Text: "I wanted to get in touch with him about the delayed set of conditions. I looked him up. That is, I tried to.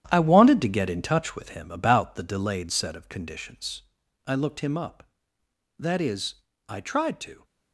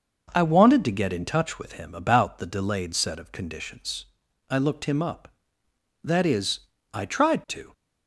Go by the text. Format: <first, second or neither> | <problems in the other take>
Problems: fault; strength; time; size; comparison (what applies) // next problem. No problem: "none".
second | gets quieter; strong; throughout; 9.5 dB